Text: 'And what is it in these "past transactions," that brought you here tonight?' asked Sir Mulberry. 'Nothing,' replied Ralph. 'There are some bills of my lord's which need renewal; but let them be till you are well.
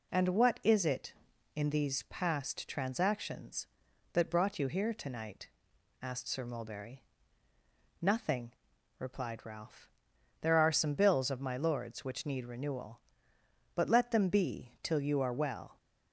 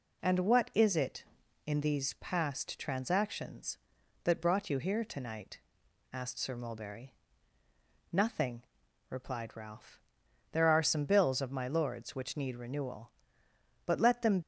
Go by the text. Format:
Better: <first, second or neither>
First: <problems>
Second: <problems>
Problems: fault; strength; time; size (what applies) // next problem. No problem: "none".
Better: first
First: none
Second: stops before "be till you are well"; at 14.4 s